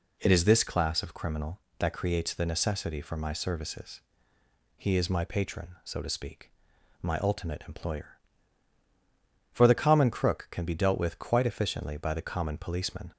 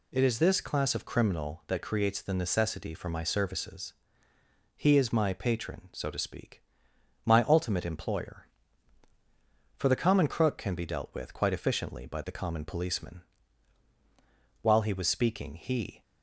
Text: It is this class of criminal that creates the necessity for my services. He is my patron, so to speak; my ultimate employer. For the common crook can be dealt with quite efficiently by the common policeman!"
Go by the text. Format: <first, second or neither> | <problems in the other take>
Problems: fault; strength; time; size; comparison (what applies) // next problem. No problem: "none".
first | goes on to say "While he was speaking he"; from 14.6 s on; 1.4 s long